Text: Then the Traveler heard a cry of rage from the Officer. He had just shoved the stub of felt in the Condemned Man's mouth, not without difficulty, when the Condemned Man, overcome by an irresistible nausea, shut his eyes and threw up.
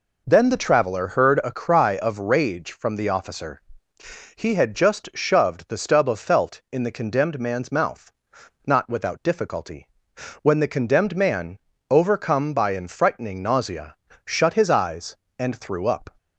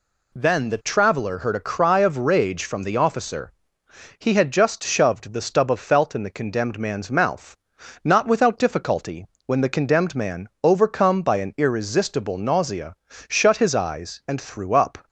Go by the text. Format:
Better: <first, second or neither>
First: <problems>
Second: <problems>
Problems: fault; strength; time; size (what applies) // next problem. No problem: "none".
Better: second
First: says "frightening" for "irresistible"; at 12.8 s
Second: none